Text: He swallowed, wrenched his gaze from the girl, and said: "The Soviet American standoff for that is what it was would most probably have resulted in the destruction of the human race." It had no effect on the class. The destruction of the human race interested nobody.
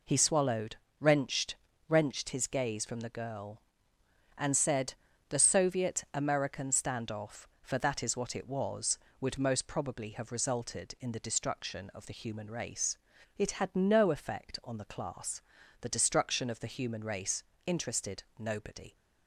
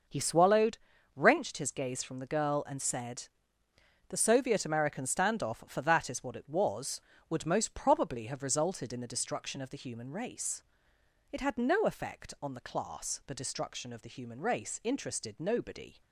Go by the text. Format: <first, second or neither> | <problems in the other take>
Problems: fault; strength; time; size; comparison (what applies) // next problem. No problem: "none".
second | says "wrenched" twice; at 1.8 s // pauses between "race" and "interested"; slight; at 17.4 s; 0.24 s long // pauses between "interested" and "nobody"; slight; at 18.2 s; 0.16 s long